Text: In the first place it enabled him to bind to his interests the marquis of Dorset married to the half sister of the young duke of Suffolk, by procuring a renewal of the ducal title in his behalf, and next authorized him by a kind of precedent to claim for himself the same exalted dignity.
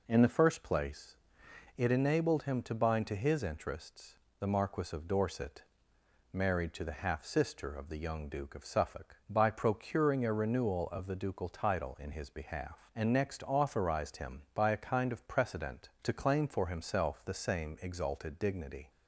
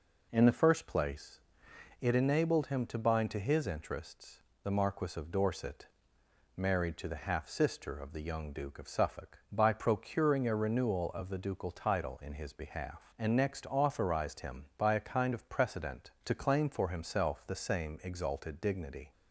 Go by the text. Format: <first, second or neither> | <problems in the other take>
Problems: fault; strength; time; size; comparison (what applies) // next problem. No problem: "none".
neither | pauses between "place" and "it"; noticeable; the same in both // pauses between "interests" and "the"; slight; the same in both // pauses between "Dorset" and "married"; noticeable; the same in both